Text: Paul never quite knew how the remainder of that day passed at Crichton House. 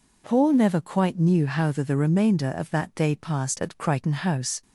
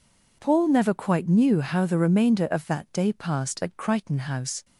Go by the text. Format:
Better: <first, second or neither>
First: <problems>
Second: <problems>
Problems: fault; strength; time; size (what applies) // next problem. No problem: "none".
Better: second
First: says "the" twice; at 1.8 s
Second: none